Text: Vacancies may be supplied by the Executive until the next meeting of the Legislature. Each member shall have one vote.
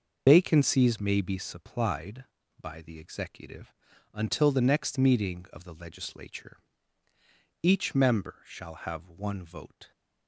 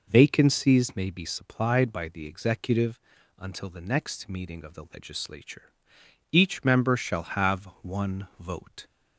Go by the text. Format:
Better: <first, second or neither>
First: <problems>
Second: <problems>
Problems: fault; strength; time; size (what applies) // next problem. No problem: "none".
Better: second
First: loses the start of "Vacancies"; at 0.2 s; 100 ms // pauses between "Executive" and "until"; at 3.7 s; 0.42 s long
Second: pauses between "Executive" and "until"; at 3.0 s; 0.38 s long